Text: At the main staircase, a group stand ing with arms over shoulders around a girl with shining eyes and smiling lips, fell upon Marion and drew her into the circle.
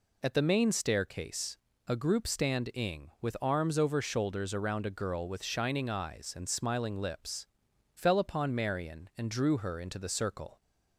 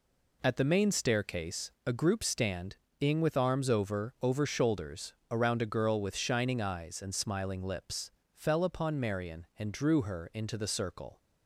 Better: first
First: none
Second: pauses between "stand" and "ing"; slight; at 2.7 s; 0.24 s long // says "over" twice; at 4.2 s // pauses between "shoulders" and "around"; slight; at 5.1 s; 0.16 s long

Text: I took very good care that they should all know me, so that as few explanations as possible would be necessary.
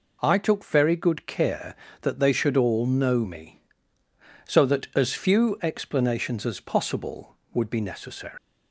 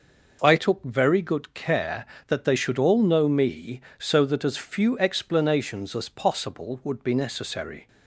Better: second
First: leaves "necessary" unfinished; at 8.3 s; 210 ms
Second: none

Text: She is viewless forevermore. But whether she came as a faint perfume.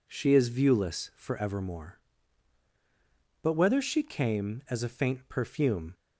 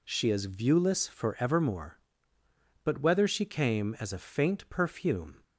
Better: neither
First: none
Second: none

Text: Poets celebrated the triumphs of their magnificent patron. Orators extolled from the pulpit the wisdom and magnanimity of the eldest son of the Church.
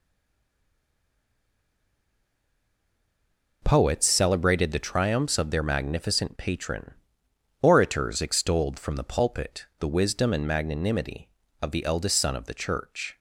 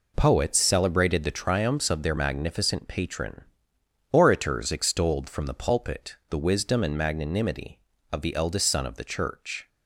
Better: second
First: stays silent before the first word; strong; until 3.6 s; 3.6 s long // pauses between "pulpit" and "the"; slight; at 9.6 s; 0.16 s long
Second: pauses between "pulpit" and "the"; slight; at 6.1 s; 0.16 s long

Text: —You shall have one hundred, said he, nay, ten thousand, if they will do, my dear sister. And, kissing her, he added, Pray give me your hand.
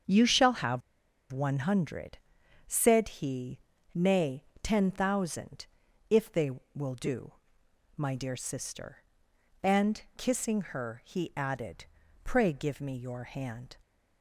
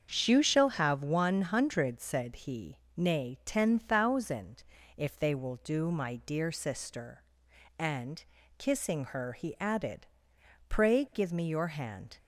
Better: second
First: starts louder than the rest; until 1.5 s; 7 dB // pauses between "have" and "one"; noticeable; at 0.8 s; 0.51 s long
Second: starts louder than the rest; until 1.2 s; 7 dB

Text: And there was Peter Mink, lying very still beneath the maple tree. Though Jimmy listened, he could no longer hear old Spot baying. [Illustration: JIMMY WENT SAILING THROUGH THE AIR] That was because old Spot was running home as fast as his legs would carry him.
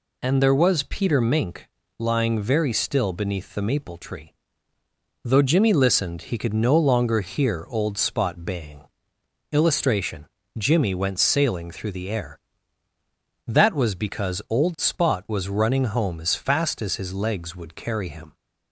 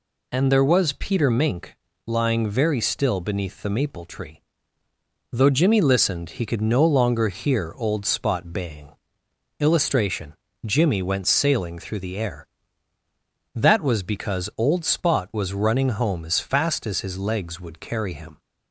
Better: neither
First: none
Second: none

